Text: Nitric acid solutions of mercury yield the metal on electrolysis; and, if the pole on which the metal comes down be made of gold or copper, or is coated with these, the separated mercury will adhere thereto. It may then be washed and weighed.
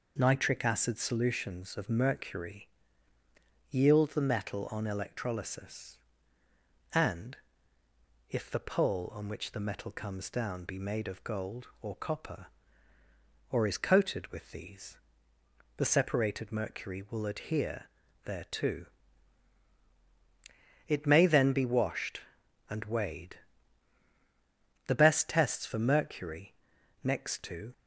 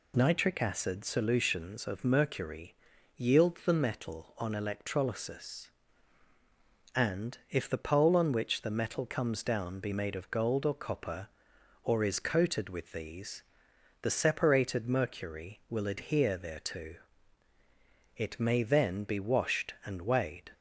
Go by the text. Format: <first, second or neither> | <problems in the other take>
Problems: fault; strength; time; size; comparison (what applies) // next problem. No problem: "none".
second | pauses between "mercury" and "yield"; at 2.6 s; 1.0 s long; also in the second // pauses between "adhere" and "thereto"; at 17.8 s; 0.40 s long // goes on to say "The best tests for mercury next to"; strong; from 24.8 s on; 2.8 s long